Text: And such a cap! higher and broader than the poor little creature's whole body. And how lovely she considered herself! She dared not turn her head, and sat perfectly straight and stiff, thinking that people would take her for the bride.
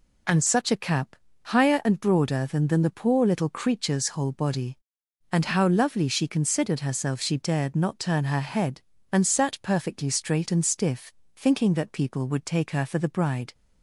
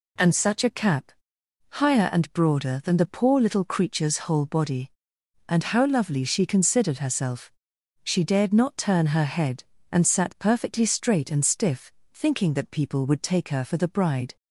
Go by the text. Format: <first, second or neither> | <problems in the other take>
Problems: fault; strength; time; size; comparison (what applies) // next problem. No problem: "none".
second | says "than" twice; at 2.6 s